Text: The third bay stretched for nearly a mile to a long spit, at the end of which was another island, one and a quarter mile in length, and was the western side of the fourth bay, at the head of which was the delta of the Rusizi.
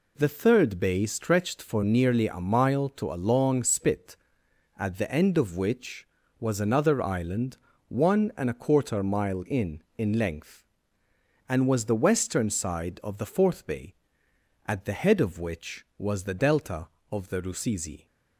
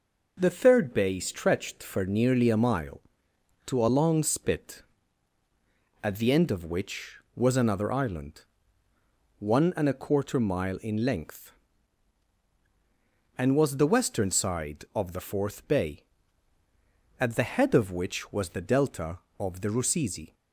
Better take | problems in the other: second | says "in" twice; at 9.9 s

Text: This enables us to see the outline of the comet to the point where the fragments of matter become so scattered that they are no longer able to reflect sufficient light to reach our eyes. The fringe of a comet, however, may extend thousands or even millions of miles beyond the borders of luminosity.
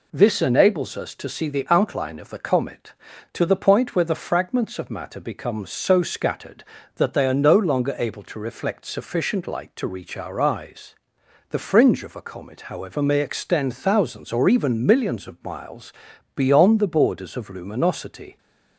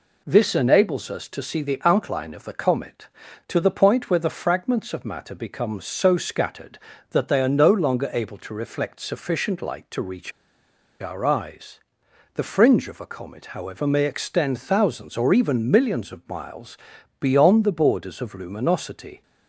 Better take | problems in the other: first | pauses between "reach" and "our"; noticeable; at 10.3 s; 0.70 s long // pauses between "miles" and "beyond"; at 16.7 s; 0.42 s long; also in the first

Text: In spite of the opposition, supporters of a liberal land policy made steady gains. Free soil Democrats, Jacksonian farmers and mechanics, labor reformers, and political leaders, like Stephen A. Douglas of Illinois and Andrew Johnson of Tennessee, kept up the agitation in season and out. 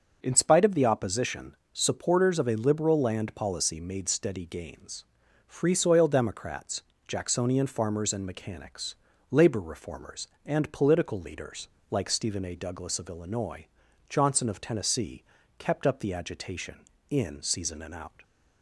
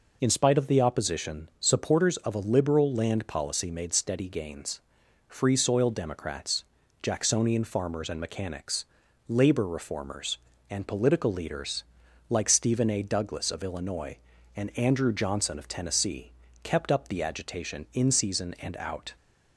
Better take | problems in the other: second | skips "and Andrew"; at 13.8 s

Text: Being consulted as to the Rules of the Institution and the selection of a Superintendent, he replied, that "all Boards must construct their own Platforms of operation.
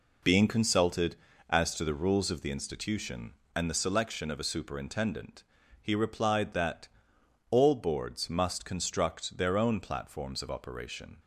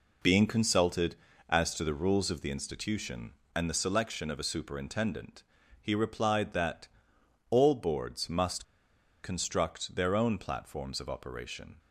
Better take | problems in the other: first | pauses between "that" and "all"; noticeable; at 6.8 s; 0.64 s long; noticeable in the first // pauses between "must" and "construct"; noticeable; at 8.6 s; 0.58 s long

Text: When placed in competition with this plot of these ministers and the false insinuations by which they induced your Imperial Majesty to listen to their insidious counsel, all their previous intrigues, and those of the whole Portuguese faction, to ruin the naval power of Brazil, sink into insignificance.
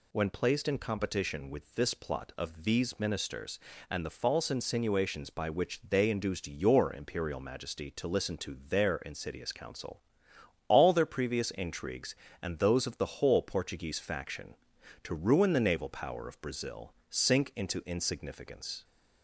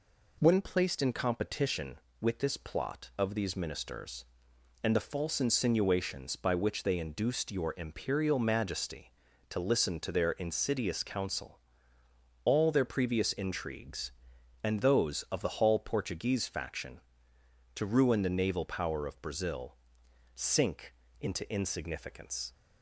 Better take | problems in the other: first | says "hall" for "whole"; at 15.5 s // pauses between "sink" and "into"; slight; at 20.9 s; 0.26 s long

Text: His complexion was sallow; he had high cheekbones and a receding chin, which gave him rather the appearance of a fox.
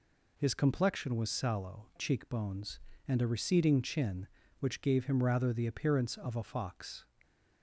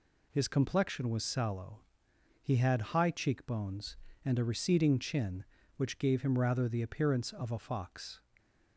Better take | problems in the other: second | skips "he had high"; at 1.9 s

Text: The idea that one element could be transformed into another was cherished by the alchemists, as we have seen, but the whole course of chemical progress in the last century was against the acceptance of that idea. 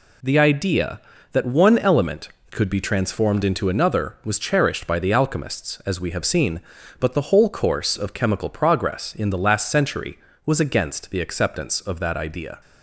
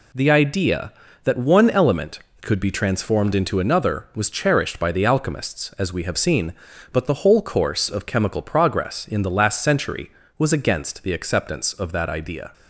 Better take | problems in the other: neither | none

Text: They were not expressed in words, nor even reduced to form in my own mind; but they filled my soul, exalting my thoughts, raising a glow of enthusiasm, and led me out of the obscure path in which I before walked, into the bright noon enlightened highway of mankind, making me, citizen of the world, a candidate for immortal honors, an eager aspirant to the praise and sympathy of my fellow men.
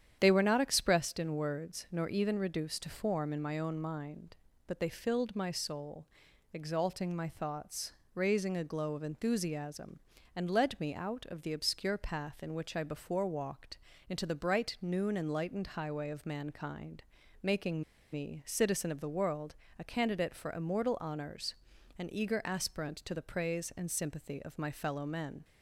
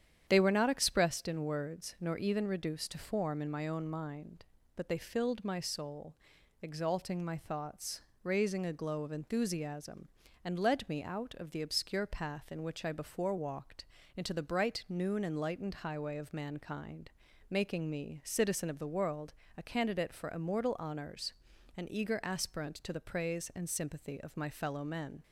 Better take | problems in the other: second | starts louder than the rest; strong; until 1.2 s; 9.5 dB; strong in the second // pauses between "making" and "me"; slight; at 17.8 s; 0.31 s long

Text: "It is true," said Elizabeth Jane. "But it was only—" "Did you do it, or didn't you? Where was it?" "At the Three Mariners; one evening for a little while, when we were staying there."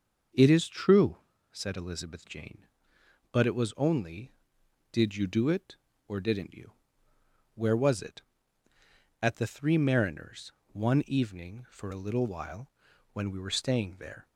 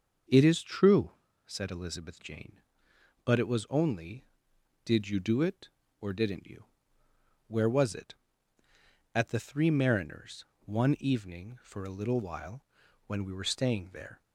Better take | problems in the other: neither | starts louder than the rest; the same in both

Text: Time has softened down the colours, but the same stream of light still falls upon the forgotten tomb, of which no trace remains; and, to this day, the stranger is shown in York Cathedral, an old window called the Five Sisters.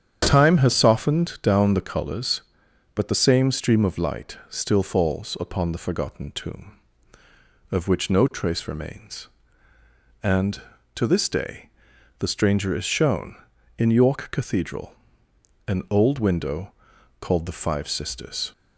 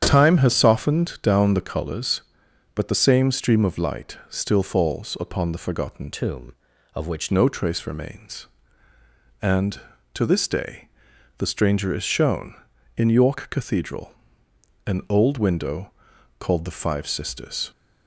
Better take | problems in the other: first | starts louder than the rest; strong; until 1.0 s; 8.5 dB; strong in the first // changes voice from "tomb" to "which"; from 6.1 to 7.3 s; 1.2 s long // pauses between "window" and "called"; noticeable; at 15.9 s; 0.50 s long; noticeable in the first

